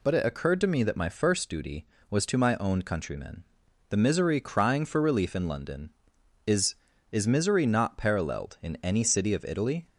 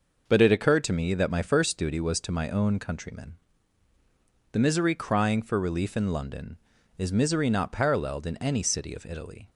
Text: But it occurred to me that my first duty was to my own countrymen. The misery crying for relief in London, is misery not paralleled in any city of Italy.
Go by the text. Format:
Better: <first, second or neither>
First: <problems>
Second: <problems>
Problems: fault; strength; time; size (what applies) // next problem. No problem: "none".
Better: second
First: says "is" twice; at 7.1 s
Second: none